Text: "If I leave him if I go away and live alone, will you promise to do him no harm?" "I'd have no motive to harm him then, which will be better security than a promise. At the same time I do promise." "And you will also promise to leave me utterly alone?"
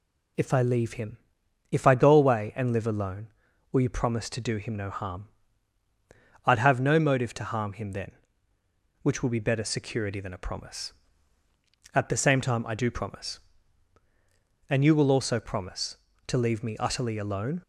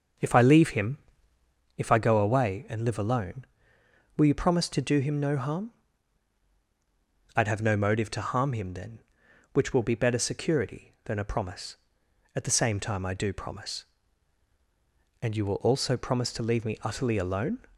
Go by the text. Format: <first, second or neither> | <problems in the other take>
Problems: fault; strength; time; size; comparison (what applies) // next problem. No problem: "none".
first | starts louder than the rest; until 1.6 s; 6.5 dB // pauses between "him" and "if"; noticeable; at 0.9 s; 0.78 s long; noticeable in the first